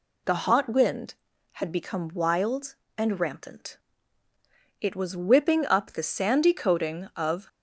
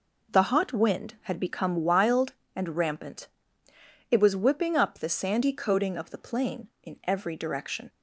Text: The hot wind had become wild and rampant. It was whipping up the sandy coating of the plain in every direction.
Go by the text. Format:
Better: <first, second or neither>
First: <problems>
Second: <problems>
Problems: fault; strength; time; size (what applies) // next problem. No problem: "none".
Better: second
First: stops before "the plain in every direction"; at 7.4 s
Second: none